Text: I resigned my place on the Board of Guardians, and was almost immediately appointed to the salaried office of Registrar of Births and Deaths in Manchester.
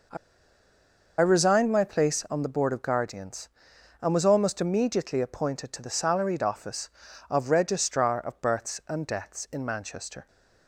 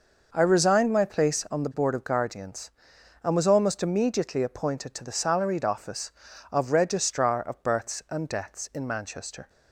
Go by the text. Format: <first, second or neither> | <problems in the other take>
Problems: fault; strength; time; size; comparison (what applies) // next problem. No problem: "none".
second | pauses between "I" and "resigned"; at 0.1 s; 1.0 s long